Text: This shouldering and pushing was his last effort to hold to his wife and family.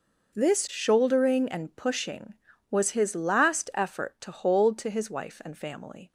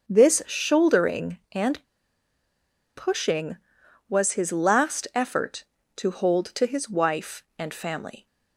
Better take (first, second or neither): first